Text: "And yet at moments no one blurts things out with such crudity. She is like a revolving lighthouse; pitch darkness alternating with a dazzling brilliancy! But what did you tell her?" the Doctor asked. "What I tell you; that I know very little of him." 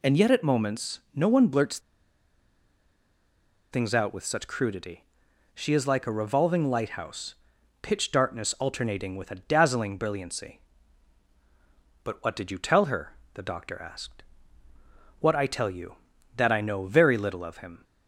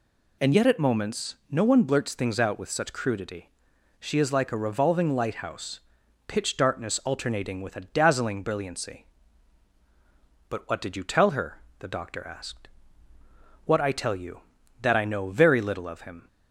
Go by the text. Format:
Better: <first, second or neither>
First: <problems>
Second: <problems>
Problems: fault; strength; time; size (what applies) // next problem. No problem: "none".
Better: second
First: pauses between "blurts" and "things"; strong; at 1.7 s; 1.9 s long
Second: none